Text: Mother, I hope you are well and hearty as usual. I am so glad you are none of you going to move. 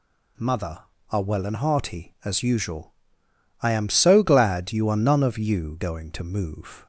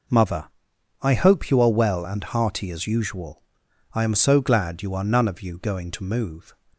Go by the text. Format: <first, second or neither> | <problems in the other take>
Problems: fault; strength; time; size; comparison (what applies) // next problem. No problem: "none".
second | skips "I hope you"; at 0.9 s